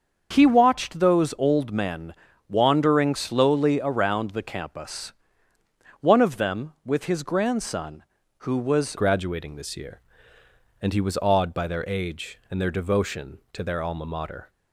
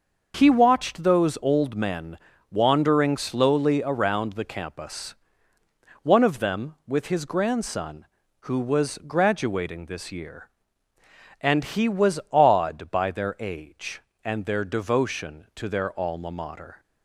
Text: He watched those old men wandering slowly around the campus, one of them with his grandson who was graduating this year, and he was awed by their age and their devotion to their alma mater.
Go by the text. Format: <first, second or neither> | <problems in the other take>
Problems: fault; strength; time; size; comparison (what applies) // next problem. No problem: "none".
second | starts louder than the rest; until 1.3 s; 6.5 dB; noticeable in the second // pauses between "men" and "wandering"; slight; at 2.1 s; 0.34 s long; slight in the second // changes voice at "graduating"; from 8.9 s on; 5.5 s long